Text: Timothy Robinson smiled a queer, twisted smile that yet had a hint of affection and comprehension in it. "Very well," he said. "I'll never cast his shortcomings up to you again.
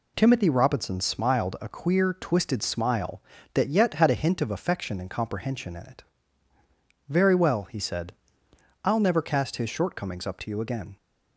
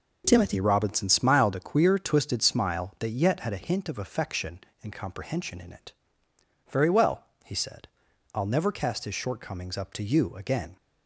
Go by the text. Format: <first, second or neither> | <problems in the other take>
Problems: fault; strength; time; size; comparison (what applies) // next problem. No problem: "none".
neither | none